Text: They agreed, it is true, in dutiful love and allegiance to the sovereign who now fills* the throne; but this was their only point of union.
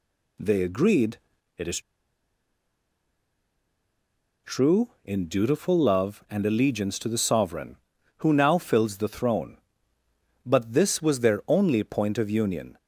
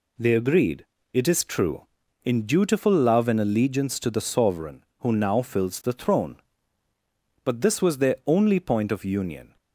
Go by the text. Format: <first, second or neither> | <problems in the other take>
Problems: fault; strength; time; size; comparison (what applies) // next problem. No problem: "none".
second | pauses between "is" and "true"; strong; at 1.7 s; 2.6 s long